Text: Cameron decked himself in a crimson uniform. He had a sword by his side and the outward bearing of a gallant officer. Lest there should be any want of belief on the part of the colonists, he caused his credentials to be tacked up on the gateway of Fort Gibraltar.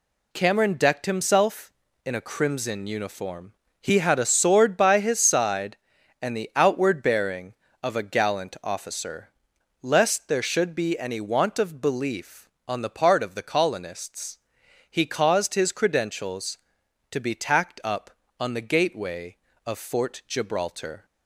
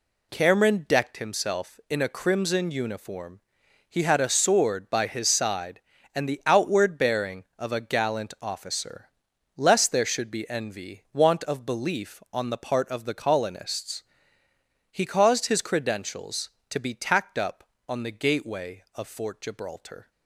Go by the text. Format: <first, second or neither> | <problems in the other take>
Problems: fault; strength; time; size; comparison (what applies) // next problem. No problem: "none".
first | says "envy" for "any"; at 10.4 s